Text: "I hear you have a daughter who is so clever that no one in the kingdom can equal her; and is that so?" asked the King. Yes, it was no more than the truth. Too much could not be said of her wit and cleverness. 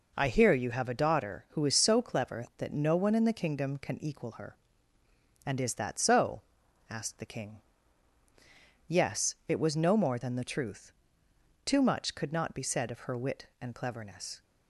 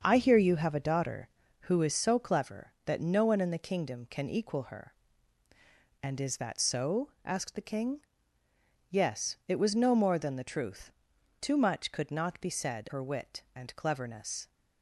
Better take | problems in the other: first | starts louder than the rest; until 1.0 s; 6.5 dB // skips "of"; at 12.8 s

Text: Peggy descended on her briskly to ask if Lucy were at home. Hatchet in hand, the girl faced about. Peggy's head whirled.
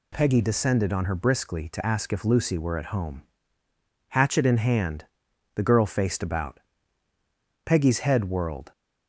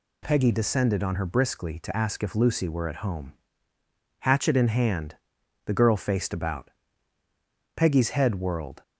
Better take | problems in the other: neither | none

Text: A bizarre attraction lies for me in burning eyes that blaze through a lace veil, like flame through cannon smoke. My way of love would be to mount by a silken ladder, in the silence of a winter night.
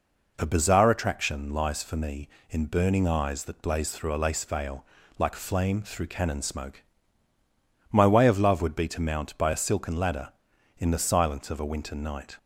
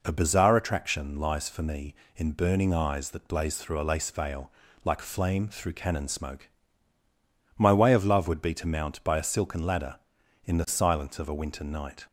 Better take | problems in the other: neither | none

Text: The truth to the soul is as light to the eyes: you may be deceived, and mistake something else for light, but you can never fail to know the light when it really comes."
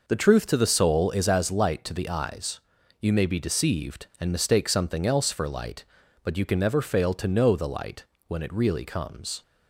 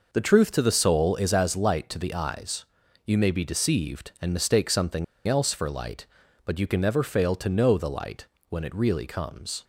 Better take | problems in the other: first | pauses between "something" and "else"; slight; at 5.0 s; 0.22 s long // pauses between "light" and "when"; slight; at 8.2 s; 0.22 s long; slight in the first

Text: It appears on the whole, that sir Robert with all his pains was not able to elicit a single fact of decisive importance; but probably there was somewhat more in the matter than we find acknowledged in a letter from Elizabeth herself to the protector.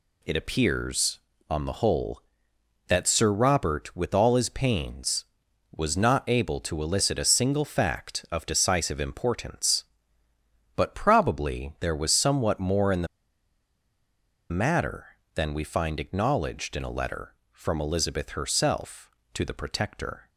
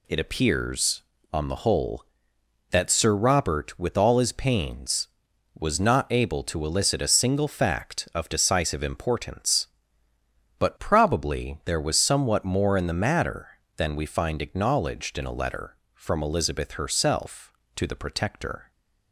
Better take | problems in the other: second | pauses between "the" and "matter"; strong; at 13.0 s; 1.4 s long

